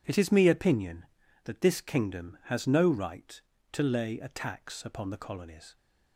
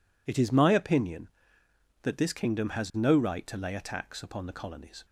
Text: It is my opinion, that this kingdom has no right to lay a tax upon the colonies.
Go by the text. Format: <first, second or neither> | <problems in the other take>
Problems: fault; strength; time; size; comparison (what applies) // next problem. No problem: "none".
second | says "me" for "my"; at 0.3 s